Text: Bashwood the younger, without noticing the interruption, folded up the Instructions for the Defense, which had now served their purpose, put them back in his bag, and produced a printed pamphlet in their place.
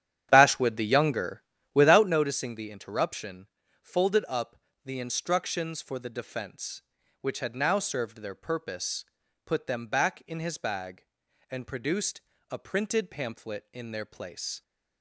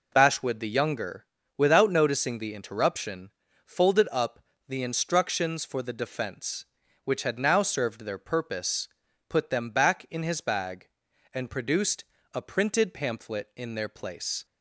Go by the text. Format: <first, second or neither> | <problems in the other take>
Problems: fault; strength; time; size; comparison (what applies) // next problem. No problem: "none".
second | starts louder than the rest; strong; until 2.2 s; 9.5 dB // pauses between "up" and "the"; slight; at 4.5 s; 0.28 s long; slight in the second // pauses between "produced" and "a"; slight; at 12.2 s; 0.28 s long; slight in the second